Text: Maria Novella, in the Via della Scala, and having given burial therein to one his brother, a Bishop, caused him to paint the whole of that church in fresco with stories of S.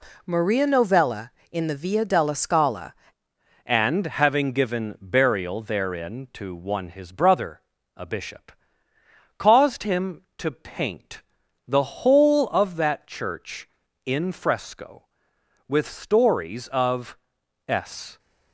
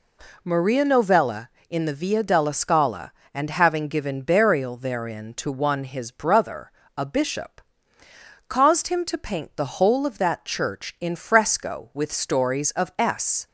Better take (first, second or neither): second